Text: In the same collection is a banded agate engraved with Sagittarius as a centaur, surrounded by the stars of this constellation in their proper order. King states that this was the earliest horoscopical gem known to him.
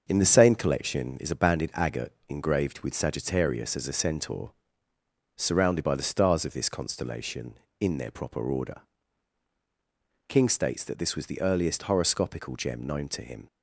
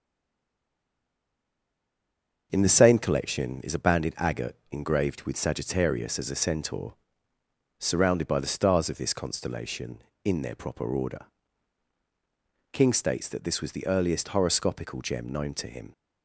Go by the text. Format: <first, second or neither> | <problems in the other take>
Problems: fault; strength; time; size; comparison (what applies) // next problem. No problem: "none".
first | stays silent before the first word; until 2.5 s; 2.5 s long // starts louder than the rest; until 3.5 s; 6.5 dB; also in the first // pauses between "agate" and "engraved"; slight; at 4.5 s; 0.15 s long; slight in the first